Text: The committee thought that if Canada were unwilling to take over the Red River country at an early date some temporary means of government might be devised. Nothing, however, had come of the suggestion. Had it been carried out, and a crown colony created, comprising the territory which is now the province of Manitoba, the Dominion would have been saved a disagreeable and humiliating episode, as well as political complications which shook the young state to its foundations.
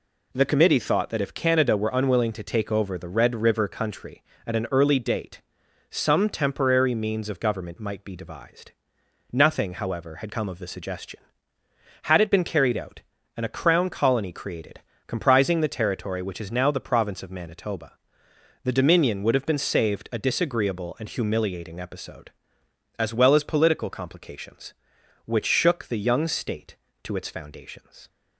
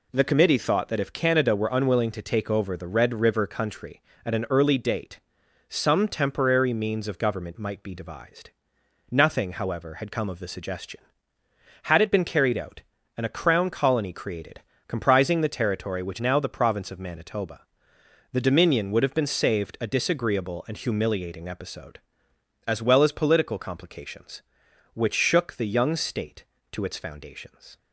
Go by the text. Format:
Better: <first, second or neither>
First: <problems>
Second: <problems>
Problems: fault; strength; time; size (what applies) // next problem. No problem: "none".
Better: first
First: pauses between "date" and "some"; noticeable; at 5.4 s; 0.52 s long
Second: pauses between "date" and "some"; noticeable; at 5.1 s; 0.52 s long // skips "is"; at 16.1 s